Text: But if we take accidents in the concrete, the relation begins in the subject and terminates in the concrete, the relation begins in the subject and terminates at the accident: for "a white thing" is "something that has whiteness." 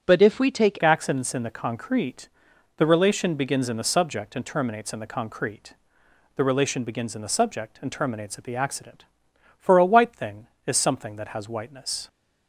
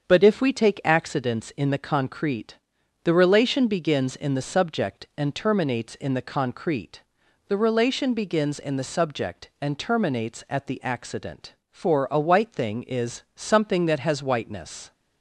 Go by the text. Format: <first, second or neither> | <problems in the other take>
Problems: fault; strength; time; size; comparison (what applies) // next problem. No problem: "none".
second | starts louder than the rest; until 1.0 s; 7 dB; also in the second // changes voice at "accidents"; from 0.8 s on; 11.2 s long